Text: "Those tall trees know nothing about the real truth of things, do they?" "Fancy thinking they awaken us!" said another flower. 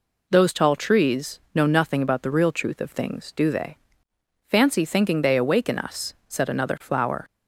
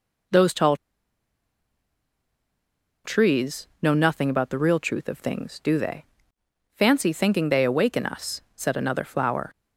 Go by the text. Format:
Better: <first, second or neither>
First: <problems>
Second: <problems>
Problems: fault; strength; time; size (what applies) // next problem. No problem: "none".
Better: first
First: none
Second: pauses between "tall" and "trees"; strong; at 0.7 s; 2.2 s long